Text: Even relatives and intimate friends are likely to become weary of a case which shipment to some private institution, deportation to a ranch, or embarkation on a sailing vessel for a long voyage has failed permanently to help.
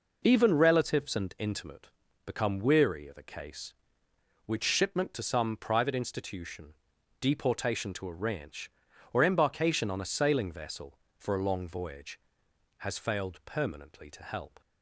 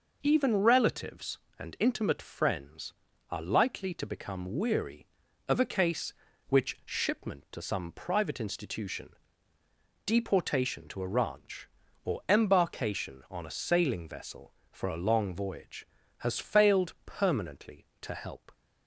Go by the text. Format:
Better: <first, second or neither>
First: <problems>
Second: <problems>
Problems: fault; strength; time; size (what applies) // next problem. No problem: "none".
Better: second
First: skips "friends are likely to"; at 2.0 s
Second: none